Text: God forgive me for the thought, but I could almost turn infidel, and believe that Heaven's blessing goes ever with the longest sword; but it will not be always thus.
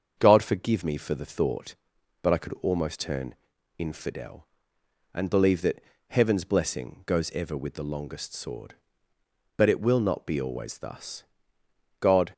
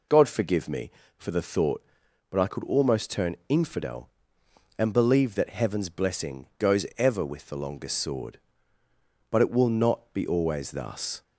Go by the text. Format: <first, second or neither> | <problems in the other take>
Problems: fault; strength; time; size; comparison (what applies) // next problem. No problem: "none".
second | starts louder than the rest; until 1.2 s; 7 dB // pauses between "turn" and "infidel"; at 3.3 s; 0.44 s long // pauses between "that" and "Heaven's"; slight; at 5.8 s; 0.30 s long // goes on to say "God"; slight; from 12.0 s on; 0.32 s long